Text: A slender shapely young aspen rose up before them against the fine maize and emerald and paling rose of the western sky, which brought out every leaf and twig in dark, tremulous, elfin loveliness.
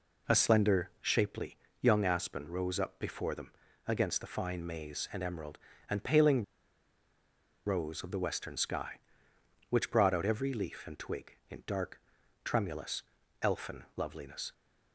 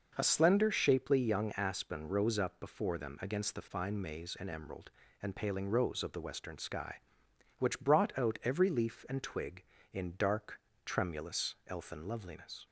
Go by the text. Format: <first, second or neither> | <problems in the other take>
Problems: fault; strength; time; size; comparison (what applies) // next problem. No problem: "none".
second | pauses between "shapely" and "young"; slight; at 1.5 s; 0.24 s long // pauses between "them" and "against"; slight; at 3.5 s; 0.36 s long // pauses between "paling" and "rose"; at 6.4 s; 1.2 s long